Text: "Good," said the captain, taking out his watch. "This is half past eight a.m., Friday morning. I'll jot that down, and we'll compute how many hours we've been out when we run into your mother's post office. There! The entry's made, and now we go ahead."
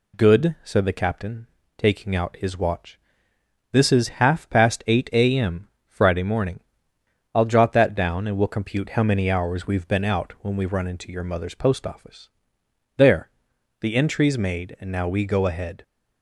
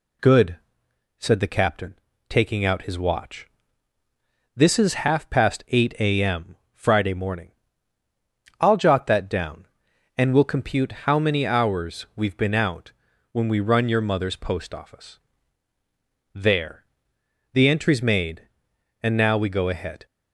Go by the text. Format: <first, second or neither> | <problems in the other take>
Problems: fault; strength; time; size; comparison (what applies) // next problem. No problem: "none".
first | pauses between "out" and "when"; at 12.9 s; 0.40 s long // skips "into"; at 13.8 s